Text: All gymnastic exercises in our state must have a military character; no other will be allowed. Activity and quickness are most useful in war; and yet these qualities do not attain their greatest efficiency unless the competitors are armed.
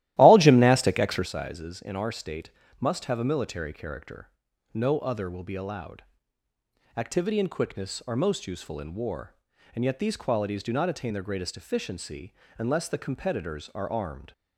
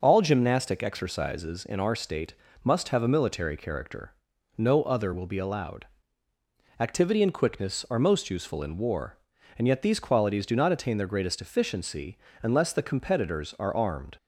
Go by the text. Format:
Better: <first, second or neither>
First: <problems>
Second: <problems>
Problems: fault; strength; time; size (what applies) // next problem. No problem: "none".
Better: second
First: starts louder than the rest; strong; until 1.3 s; 14.5 dB // pauses between "state" and "must"; slight; at 2.4 s; 0.32 s long // pauses between "efficiency" and "unless"; slight; at 12.3 s; 0.24 s long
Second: pauses between "state" and "must"; slight; at 2.3 s; 0.32 s long // pauses between "efficiency" and "unless"; slight; at 12.1 s; 0.24 s long